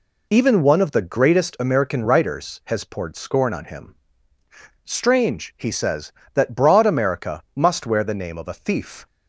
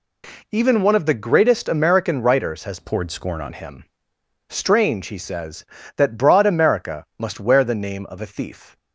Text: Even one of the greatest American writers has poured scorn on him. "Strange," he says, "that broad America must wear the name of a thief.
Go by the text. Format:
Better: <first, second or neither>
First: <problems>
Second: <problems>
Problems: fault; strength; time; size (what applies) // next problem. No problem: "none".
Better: first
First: none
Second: changes voice from "poured" to "on"; from 2.7 to 3.5 s; 0.8 s long